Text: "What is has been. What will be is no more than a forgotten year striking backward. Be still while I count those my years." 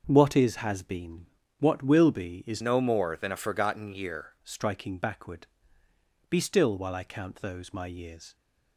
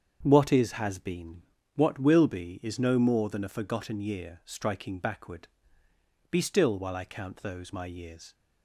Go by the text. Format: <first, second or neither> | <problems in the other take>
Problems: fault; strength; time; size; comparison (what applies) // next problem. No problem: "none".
second | starts louder than the rest; until 1.0 s; 6.5 dB; strong in the second // changes voice from "no" to "year"; from 2.6 to 4.3 s; 1.7 s long